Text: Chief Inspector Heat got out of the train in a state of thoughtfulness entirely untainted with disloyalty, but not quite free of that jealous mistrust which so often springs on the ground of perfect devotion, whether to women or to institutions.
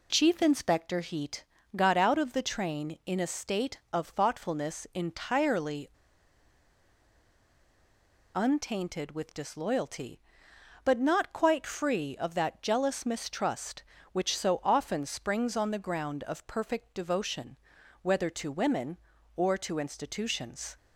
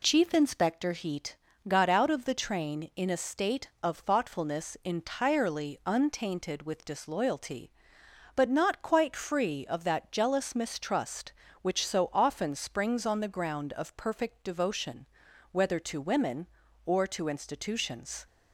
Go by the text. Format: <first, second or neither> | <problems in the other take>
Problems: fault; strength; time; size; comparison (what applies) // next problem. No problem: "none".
second | pauses between "Heat" and "got"; slight; at 1.4 s; 0.28 s long; slight in the second // pauses between "entirely" and "untainted"; strong; at 5.8 s; 2.4 s long